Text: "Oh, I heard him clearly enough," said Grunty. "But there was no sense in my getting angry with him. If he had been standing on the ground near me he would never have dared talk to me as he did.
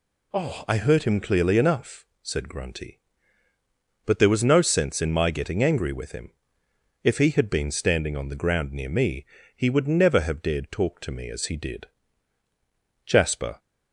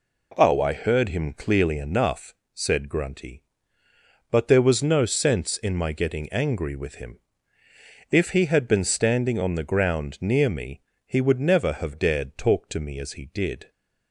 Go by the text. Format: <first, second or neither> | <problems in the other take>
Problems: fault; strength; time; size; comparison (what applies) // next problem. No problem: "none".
second | pauses between "me" and "he"; slight; at 9.2 s; 0.32 s long; slight in the second // goes on to say "Jasper"; from 13.0 s on; 0.52 s long